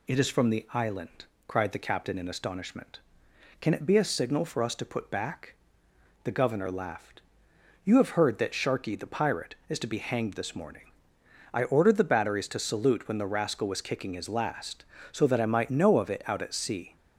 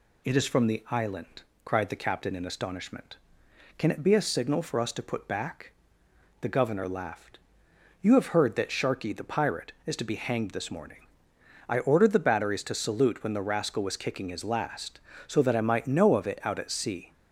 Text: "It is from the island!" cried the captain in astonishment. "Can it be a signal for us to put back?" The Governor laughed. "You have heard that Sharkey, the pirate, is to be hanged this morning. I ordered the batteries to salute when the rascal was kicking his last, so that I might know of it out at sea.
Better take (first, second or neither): neither